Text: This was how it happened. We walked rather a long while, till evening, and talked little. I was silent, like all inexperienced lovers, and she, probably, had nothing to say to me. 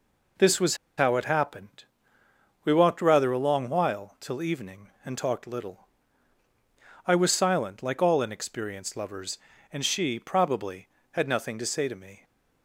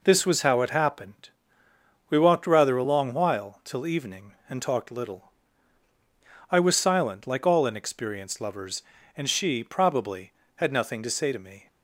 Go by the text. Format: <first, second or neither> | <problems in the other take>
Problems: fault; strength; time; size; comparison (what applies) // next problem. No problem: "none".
second | pauses between "was" and "how"; slight; at 0.7 s; 0.21 s long